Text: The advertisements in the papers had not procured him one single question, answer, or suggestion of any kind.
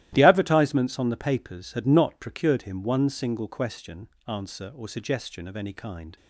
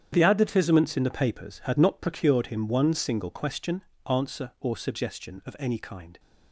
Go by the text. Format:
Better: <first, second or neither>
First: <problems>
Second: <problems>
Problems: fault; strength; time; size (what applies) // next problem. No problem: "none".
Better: second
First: starts louder than the rest; strong; until 1.1 s; 14.5 dB // says "on" for "in"; at 0.9 s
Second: starts louder than the rest; strong; until 1.1 s; 9 dB